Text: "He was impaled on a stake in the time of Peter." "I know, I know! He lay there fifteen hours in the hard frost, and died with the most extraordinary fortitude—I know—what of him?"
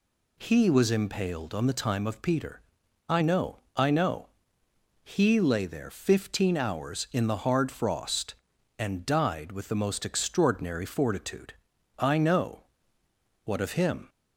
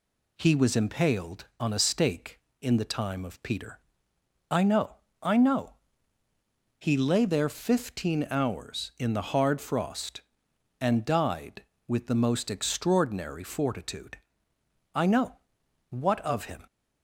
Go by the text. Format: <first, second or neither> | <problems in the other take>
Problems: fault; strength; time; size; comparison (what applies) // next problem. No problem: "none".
second | skips "a stake in"; at 1.6 s